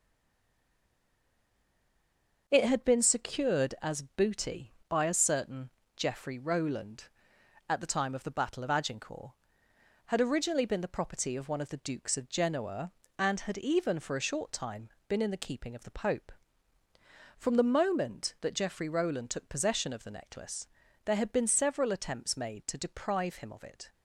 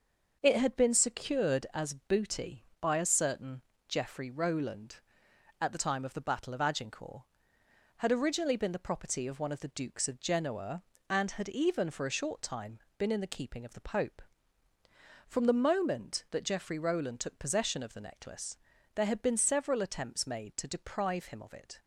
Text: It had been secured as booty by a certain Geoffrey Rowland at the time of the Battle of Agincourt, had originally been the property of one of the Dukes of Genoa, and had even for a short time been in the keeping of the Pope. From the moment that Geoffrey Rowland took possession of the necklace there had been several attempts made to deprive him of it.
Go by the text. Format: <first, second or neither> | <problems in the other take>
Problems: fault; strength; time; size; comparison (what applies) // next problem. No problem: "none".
second | stays silent before the first word; until 2.4 s; 2.4 s long // starts louder than the rest; until 3.4 s; 6 dB; also in the second // pauses between "certain" and "Geoffrey"; slight; at 5.6 s; 0.28 s long; slight in the second // pauses between "time" and "been"; slight; at 14.8 s; 0.18 s long; slight in the second // pauses between "necklace" and "there"; at 20.6 s; 0.38 s long; also in the second